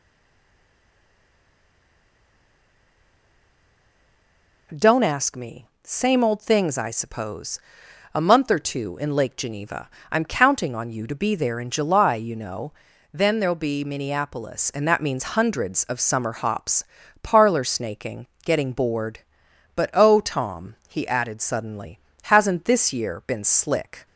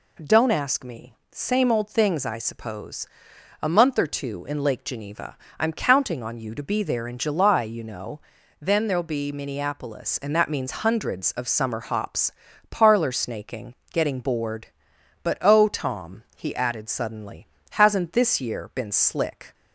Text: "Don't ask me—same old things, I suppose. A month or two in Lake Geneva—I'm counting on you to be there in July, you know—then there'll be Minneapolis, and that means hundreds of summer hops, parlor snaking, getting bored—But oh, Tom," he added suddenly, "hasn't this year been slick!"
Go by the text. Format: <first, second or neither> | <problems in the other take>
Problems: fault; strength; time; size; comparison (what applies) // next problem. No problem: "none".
second | stays silent before the first word; strong; until 4.7 s; 4.7 s long